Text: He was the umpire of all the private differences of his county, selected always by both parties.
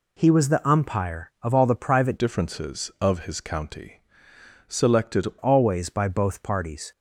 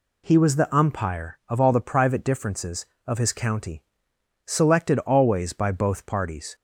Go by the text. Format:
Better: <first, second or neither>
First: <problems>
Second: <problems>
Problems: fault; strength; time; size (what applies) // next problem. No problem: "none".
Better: second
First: changes voice from "differences" to "selected"; from 2.1 to 5.2 s; 3.1 s long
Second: none